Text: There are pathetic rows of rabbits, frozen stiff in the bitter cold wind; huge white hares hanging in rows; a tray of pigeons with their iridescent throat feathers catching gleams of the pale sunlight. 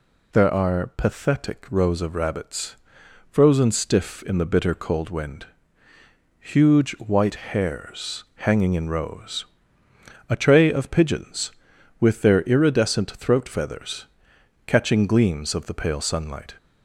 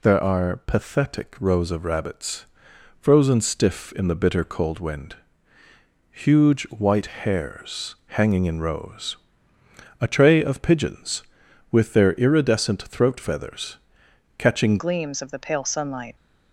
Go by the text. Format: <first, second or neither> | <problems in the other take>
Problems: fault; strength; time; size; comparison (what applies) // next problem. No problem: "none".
first | pauses between "feathers" and "catching"; noticeable; at 13.7 s; 0.58 s long; noticeable in the first // changes voice at "gleams"; from 14.7 s on; 1.4 s long